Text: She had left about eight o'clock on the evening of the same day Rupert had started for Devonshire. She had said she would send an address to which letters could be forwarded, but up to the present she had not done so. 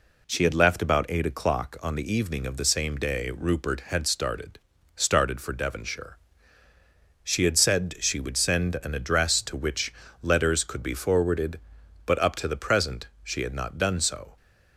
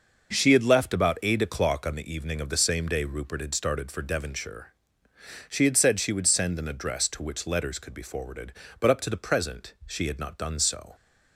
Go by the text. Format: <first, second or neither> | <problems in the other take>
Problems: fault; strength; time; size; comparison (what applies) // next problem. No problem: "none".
second | says "started" twice; at 4.9 s // pauses between "which" and "letters"; slight; at 9.9 s; 0.30 s long // pauses between "present" and "she"; slight; at 13.0 s; 0.16 s long